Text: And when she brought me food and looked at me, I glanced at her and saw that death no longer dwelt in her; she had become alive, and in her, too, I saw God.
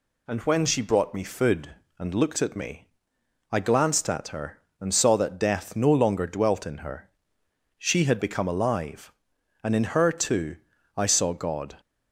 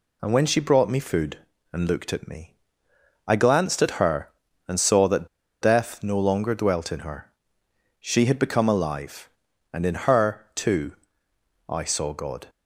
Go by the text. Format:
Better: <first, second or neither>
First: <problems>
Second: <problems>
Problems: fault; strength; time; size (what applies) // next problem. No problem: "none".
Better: first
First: none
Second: pauses between "that" and "death"; slight; at 5.2 s; 0.33 s long